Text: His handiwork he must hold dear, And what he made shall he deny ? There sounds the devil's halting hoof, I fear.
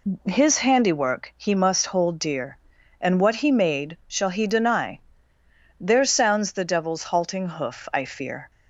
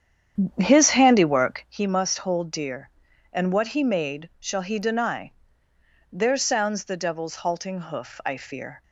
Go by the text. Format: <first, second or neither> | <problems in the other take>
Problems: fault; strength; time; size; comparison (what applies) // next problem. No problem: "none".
first | starts louder than the rest; strong; until 1.7 s; 9 dB